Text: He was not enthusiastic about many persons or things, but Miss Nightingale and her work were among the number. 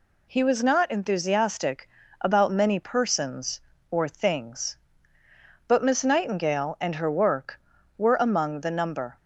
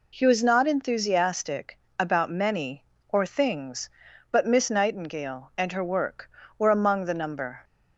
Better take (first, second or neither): first